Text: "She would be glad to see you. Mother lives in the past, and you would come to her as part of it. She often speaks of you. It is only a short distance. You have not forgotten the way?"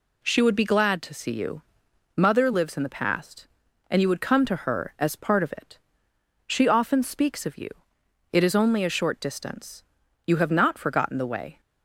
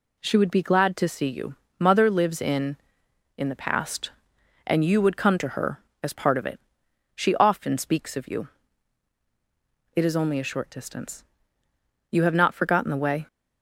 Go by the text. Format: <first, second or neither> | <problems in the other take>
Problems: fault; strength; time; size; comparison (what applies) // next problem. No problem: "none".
first | says "in" twice; at 3.3 s